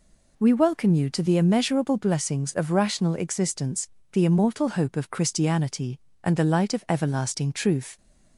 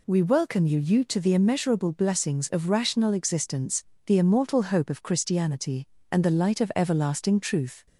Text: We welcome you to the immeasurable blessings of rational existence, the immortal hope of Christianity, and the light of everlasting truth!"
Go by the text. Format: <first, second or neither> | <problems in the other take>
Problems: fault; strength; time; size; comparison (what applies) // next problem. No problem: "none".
first | says "you" twice; at 0.7 s